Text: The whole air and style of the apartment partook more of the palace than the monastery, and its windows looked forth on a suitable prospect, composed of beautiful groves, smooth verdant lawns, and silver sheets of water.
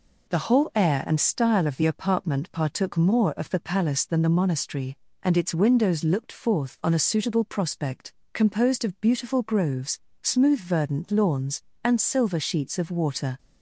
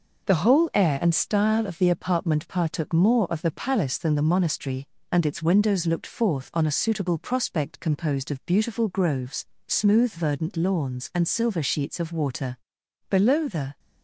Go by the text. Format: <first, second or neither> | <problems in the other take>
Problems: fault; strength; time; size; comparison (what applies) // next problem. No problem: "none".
first | goes on to say "Below the"; noticeable; from 13.0 s on; 0.70 s long